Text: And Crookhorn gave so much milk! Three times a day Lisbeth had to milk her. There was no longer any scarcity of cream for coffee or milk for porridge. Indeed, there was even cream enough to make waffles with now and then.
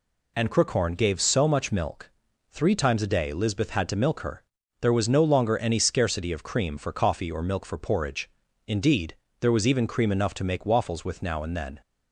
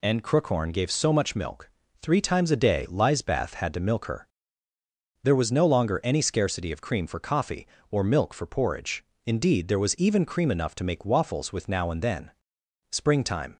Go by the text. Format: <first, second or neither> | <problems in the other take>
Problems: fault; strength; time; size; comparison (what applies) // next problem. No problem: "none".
first | goes on to say "Springtime"; noticeable; from 12.9 s on; 0.64 s long